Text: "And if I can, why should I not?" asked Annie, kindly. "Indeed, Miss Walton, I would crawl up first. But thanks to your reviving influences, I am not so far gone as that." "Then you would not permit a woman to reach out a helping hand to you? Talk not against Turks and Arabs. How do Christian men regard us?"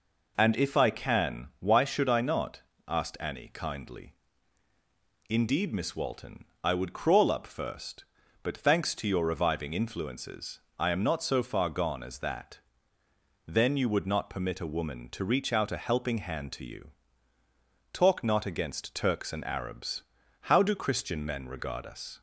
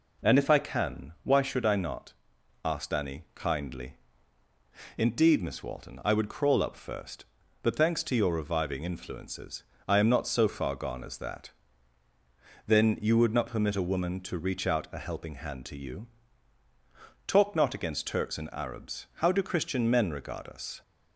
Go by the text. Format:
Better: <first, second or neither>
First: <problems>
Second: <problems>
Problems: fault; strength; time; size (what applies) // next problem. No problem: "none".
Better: neither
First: none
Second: none